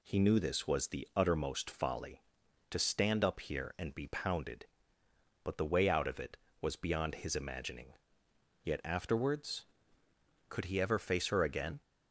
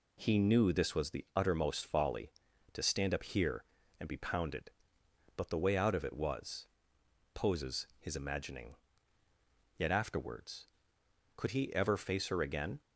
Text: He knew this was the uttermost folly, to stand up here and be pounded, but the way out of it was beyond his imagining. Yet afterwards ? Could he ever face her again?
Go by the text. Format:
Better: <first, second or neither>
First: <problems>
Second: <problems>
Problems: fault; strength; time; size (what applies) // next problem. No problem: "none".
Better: first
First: none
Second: says "poses" for "beyond"; at 7.3 s